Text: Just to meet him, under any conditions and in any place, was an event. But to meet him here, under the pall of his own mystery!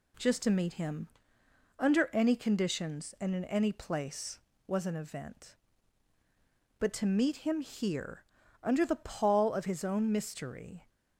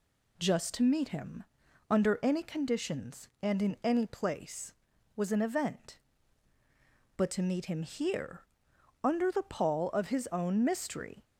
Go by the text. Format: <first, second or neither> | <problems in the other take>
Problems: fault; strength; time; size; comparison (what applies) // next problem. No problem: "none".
neither | none